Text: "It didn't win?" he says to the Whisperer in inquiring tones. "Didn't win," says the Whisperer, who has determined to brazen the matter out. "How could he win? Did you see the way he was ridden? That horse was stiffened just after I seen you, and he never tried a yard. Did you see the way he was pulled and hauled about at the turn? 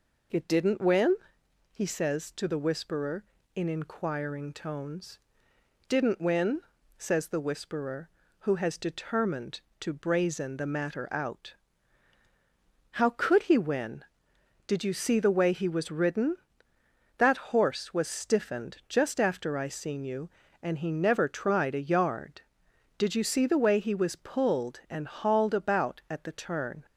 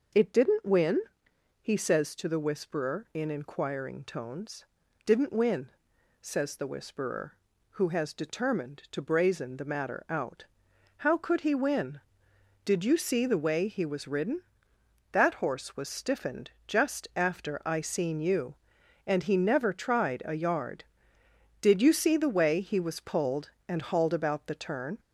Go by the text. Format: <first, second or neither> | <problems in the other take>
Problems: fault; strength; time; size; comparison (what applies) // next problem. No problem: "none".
first | pauses between "stiffened" and "just"; slight; at 16.5 s; 0.16 s long // skips "at"; at 24.4 s